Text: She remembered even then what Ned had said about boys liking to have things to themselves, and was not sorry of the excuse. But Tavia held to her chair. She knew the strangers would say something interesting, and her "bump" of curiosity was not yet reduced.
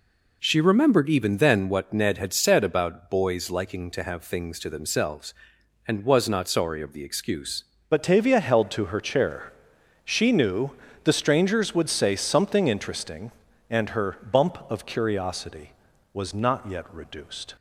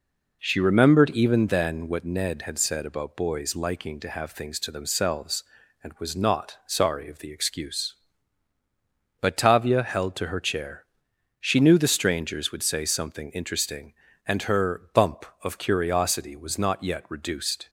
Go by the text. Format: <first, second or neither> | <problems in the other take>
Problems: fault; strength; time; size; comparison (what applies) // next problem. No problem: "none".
second | changes voice at "But"; from 7.9 s on; 9.6 s long // pauses between "knew" and "the"; slight; at 10.7 s; 0.32 s long